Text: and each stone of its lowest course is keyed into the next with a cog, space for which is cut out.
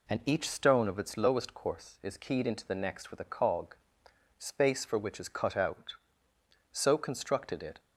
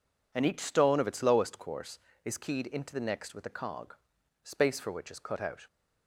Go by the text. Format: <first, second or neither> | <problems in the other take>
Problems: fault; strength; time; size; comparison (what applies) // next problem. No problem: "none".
second | goes on to say "So constructed it"; noticeable; from 6.7 s on; 1.0 s long